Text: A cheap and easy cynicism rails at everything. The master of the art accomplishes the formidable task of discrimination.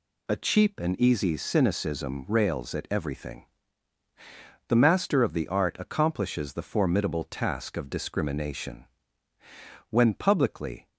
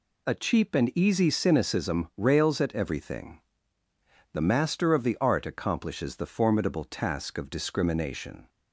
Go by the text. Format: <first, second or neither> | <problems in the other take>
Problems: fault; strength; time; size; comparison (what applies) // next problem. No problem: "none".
second | goes on to say "When publicly"; noticeable; from 9.8 s on; 0.98 s long